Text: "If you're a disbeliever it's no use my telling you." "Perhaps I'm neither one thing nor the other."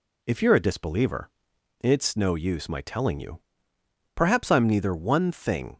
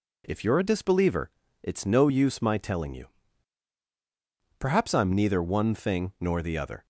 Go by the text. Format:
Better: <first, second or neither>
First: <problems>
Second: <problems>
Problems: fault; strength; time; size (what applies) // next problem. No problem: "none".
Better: second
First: pauses between "disbeliever" and "it's"; noticeable; at 1.3 s; 0.50 s long // stops before "nor the other"; at 5.7 s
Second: pauses between "disbeliever" and "it's"; slight; at 1.2 s; 0.32 s long